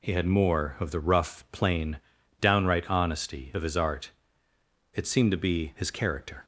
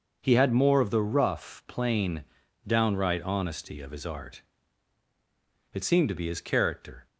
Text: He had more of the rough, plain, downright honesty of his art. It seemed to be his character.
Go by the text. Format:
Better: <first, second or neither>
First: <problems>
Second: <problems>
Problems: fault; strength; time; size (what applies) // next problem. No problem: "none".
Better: neither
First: none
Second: none